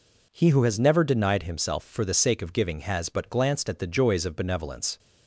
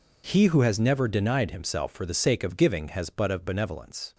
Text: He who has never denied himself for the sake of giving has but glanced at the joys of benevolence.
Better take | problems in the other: first | skips "glanced at the joys"; at 3.3 s

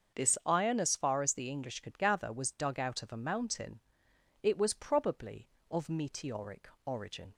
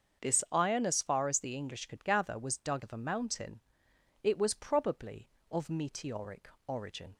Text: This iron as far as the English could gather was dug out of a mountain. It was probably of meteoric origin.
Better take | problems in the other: first | starts louder than the rest; until 1.2 s; 6.5 dB; also in the first // skips "out"; at 2.8 s // pauses between "meteoric" and "origin"; slight; at 6.4 s; 0.18 s long; slight in the first

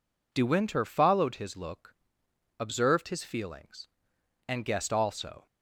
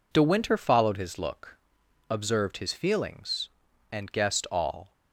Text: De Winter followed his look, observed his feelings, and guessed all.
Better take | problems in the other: second | says "also" for "all"; at 4.9 s

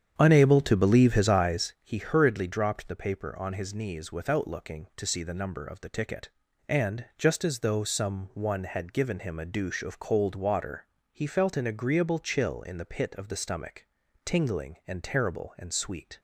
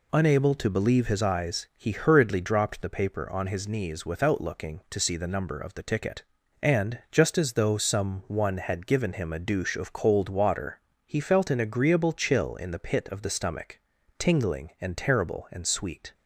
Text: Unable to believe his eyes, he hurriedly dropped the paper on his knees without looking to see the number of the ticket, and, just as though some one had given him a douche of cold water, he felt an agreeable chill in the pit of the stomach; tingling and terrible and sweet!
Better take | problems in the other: second | starts louder than the rest; strong; until 1.9 s; 8.5 dB

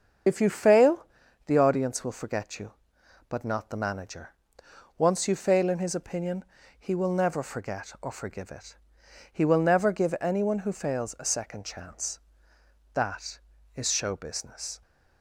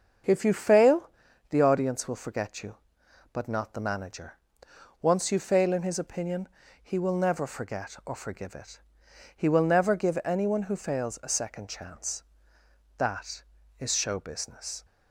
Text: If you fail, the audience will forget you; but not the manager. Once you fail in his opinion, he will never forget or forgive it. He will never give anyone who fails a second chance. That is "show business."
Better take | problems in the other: second | loses the start of "If"; at 0.2 s; 65 ms // starts louder than the rest; until 1.6 s; 7 dB; also in the second

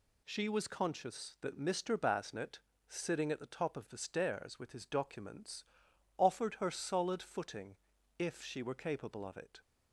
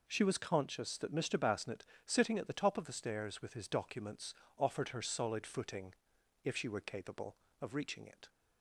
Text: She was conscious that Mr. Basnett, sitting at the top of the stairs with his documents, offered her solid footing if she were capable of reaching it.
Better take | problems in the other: second | pauses between "footing" and "if"; at 7.7 s; 0.42 s long; noticeable in the second // skips "reaching"; at 9.3 s

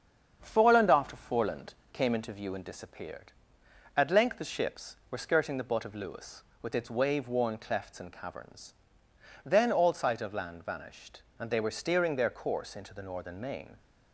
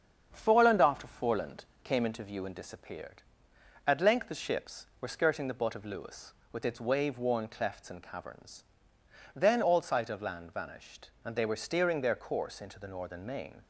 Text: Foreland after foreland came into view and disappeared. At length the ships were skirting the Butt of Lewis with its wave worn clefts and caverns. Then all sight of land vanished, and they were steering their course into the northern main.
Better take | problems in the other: neither | starts louder than the rest; strong; the same in both // pauses between "foreland" and "came"; slight; the same in both

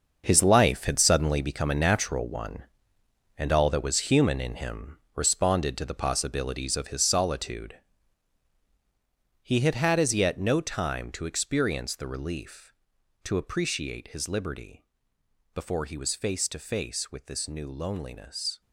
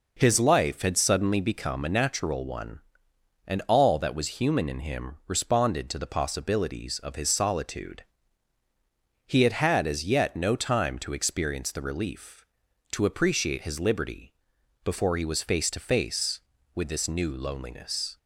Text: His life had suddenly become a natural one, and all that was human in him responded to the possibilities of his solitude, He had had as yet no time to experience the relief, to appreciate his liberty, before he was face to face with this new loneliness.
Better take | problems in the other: second | gets quieter; strong; throughout; 11.5 dB // pauses between "him" and "responded"; slight; at 4.9 s; 0.18 s long

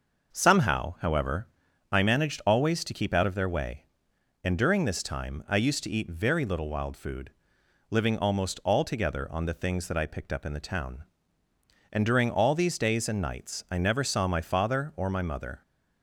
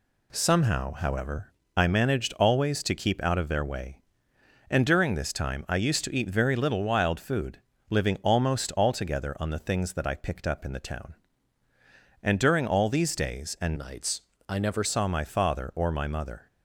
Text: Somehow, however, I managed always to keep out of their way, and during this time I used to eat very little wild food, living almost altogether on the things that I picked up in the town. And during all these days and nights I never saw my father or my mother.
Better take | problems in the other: first | changes voice from "nights" to "never"; from 13.7 to 14.8 s; 1.1 s long // pauses between "nights" and "I"; slight; at 14.2 s; 0.28 s long

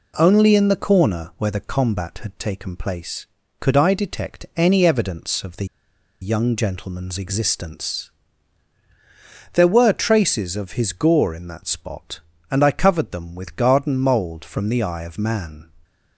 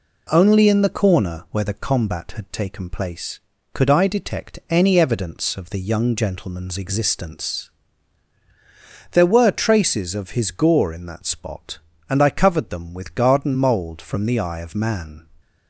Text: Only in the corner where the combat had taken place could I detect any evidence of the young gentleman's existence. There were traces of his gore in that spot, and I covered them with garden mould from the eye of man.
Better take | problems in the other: second | pauses between "the" and "young"; noticeable; at 5.6 s; 0.56 s long

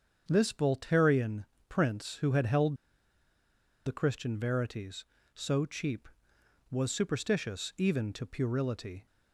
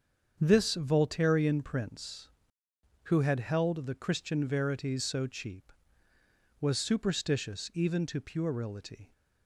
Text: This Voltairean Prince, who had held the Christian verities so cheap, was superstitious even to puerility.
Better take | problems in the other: second | starts louder than the rest; strong; until 1.2 s; 7.5 dB; strong in the second // pauses between "Voltairean" and "Prince"; slight; at 1.4 s; 0.24 s long // pauses between "held" and "the"; at 2.7 s; 1.1 s long

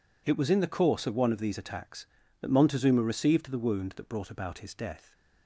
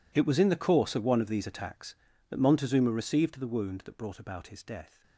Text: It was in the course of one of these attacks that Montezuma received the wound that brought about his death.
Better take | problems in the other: first | gets quieter; strong; throughout; 18.5 dB

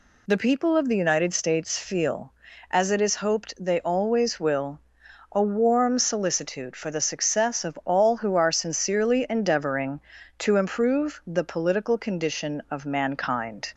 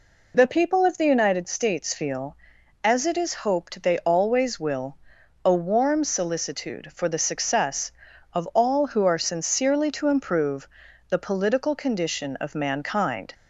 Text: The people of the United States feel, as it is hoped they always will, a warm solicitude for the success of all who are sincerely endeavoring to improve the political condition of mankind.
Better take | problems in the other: first | skips "endeavoring"; at 9.9 s // pauses between "improve" and "the"; at 10.6 s; 0.40 s long

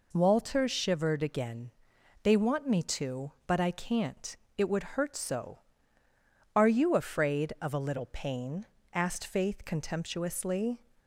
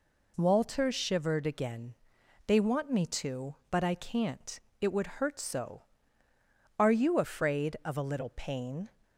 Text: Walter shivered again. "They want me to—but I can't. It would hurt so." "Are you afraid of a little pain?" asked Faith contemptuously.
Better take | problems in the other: first | stops before "asked Faith contemptuously"; at 9.0 s

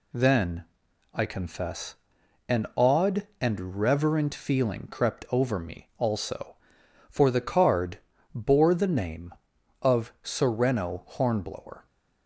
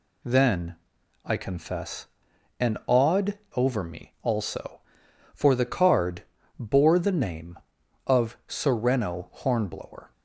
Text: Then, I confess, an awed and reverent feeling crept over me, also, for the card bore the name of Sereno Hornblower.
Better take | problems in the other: first | skips "and reverent feeling crept"; at 3.4 s // pauses between "card" and "bore"; slight; at 6.2 s; 0.34 s long; slight in the first

